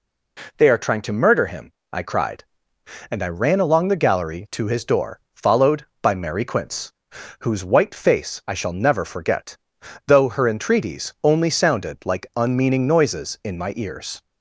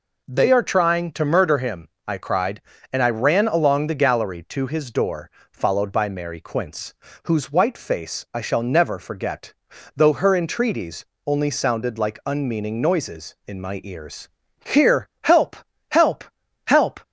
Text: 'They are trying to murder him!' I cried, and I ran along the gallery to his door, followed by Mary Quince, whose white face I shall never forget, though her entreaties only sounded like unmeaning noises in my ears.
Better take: first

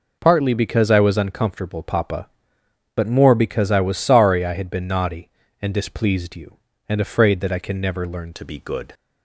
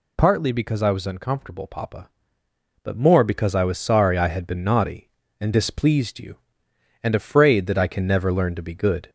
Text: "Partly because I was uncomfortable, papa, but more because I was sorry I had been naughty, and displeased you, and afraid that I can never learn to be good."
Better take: second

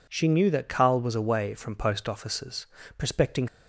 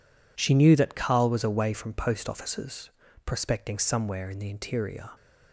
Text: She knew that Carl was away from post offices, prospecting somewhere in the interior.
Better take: second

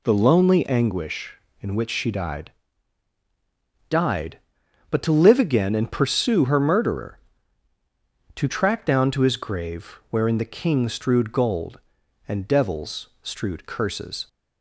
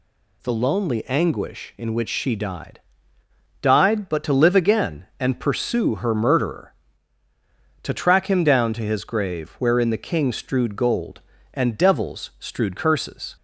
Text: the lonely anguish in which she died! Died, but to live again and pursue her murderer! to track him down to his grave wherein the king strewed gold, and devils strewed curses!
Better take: second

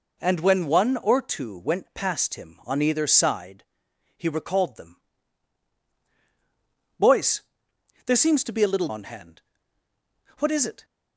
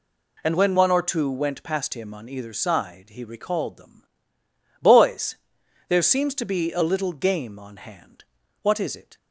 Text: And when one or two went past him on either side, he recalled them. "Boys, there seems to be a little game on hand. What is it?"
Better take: second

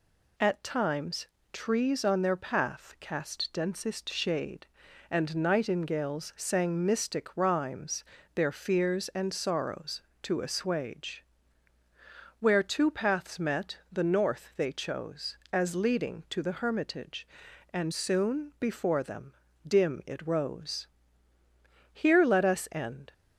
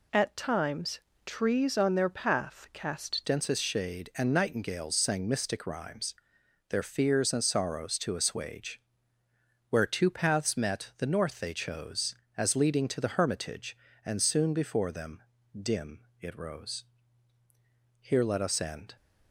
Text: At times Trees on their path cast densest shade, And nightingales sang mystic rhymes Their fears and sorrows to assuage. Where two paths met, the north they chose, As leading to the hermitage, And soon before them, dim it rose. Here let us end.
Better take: first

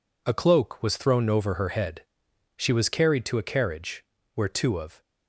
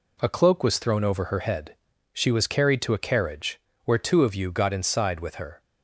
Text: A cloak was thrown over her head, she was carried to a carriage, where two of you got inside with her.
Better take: second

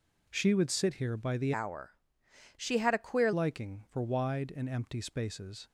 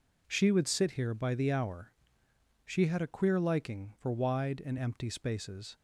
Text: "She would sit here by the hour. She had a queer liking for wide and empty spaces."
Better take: second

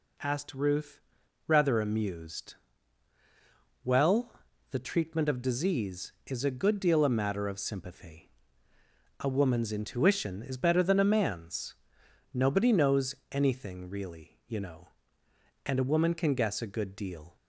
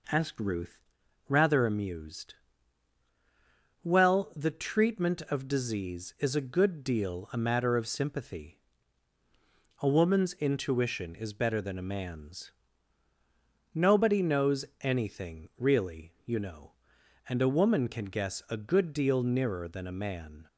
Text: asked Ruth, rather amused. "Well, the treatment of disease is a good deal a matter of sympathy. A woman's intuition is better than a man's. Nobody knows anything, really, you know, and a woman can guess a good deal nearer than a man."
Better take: second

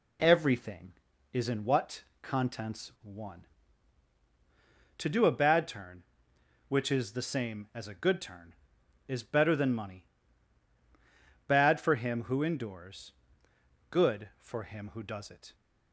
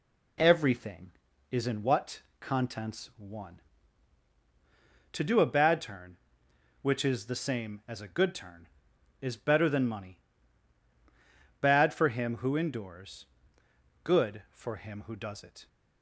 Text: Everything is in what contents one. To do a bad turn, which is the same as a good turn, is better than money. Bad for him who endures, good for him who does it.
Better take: neither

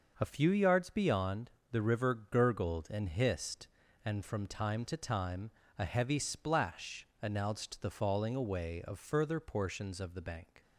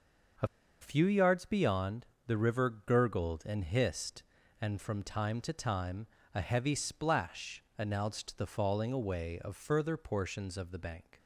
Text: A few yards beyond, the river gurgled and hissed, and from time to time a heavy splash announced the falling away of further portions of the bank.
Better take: first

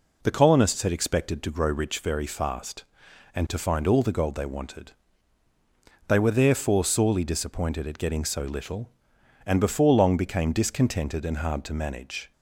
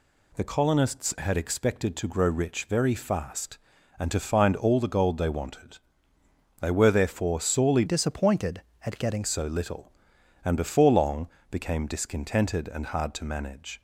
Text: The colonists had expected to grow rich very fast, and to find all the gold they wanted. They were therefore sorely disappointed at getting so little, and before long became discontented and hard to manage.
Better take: first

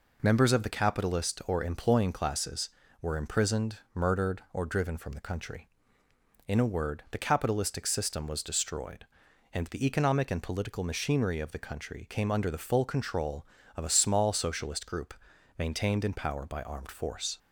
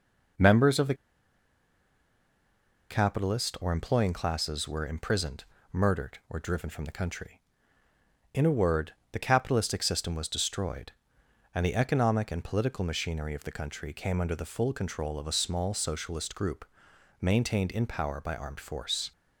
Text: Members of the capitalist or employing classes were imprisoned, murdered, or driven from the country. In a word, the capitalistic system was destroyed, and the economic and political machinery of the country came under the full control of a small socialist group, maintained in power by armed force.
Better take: first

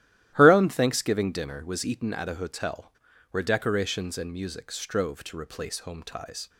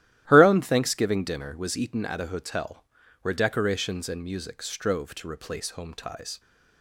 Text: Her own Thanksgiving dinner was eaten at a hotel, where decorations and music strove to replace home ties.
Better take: neither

